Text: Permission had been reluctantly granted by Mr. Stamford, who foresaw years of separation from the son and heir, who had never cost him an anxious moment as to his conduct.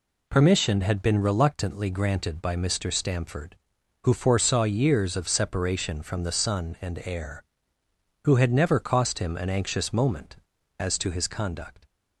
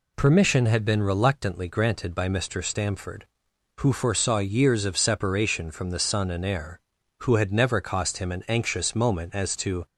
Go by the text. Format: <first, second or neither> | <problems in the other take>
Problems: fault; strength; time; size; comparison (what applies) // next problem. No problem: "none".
first | stops before "his conduct"; at 9.8 s